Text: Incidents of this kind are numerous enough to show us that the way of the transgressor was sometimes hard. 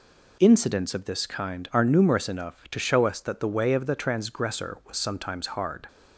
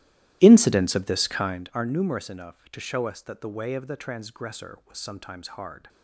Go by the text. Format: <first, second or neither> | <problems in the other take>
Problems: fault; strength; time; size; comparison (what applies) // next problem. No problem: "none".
first | starts louder than the rest; strong; until 1.8 s; 14.5 dB